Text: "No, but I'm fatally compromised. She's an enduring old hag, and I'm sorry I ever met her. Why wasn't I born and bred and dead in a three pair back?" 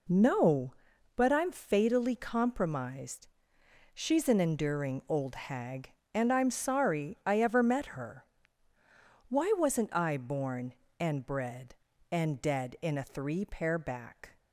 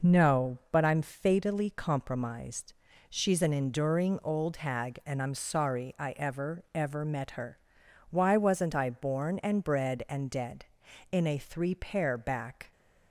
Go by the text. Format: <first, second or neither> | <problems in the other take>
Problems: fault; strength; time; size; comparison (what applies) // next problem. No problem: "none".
first | says "ever" twice; at 6.7 s